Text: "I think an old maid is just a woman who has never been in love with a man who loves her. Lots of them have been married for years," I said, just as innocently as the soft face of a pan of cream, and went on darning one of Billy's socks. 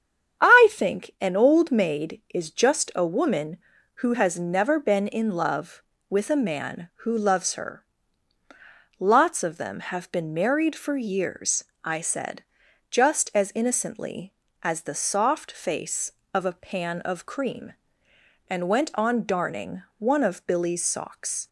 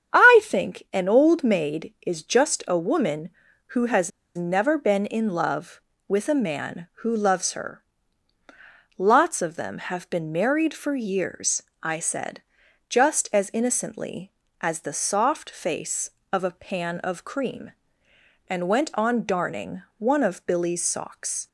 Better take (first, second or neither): first